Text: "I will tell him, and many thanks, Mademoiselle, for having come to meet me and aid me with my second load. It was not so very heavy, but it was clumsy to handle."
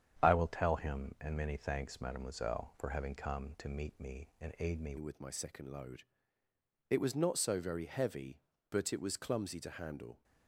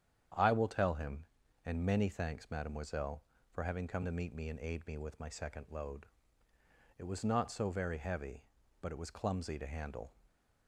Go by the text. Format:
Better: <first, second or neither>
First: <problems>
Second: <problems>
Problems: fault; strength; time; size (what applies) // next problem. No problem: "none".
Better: second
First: starts louder than the rest; strong; until 1.2 s; 8.5 dB // changes voice at "with"; from 4.9 s on; 5.3 s long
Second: starts louder than the rest; strong; until 1.7 s; 9 dB